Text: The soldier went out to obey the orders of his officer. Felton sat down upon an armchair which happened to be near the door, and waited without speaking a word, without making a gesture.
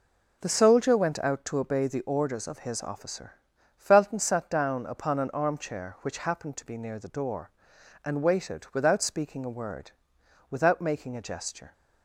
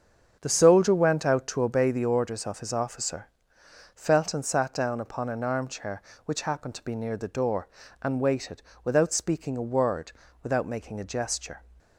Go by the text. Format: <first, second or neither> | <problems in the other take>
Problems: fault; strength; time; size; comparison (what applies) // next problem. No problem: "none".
first | starts louder than the rest; until 1.8 s; 7 dB // pauses between "waited" and "without"; slight; at 8.6 s; 0.22 s long